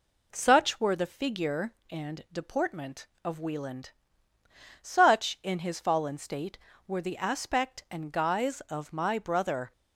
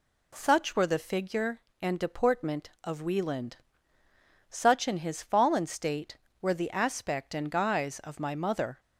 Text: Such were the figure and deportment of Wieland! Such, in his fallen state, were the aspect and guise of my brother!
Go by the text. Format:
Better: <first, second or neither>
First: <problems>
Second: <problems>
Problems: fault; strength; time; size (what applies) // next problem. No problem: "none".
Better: first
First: none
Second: says "mother" for "brother"; at 8.3 s